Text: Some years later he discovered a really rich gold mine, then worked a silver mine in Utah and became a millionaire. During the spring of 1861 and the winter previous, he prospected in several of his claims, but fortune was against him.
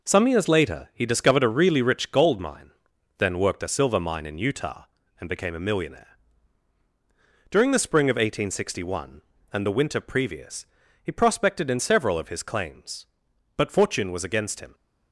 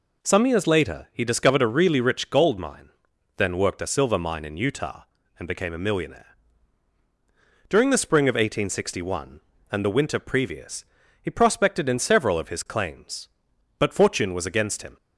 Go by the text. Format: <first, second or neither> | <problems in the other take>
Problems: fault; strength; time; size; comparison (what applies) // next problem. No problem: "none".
second | gets quieter; throughout; 6.5 dB